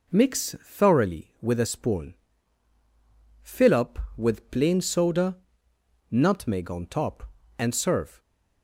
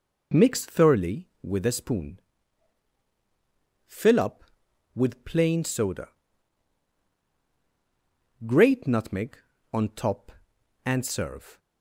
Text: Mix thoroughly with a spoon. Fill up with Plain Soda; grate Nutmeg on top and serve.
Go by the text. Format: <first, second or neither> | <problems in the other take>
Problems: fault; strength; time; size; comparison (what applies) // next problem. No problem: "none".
second | skips "grate"; at 5.7 s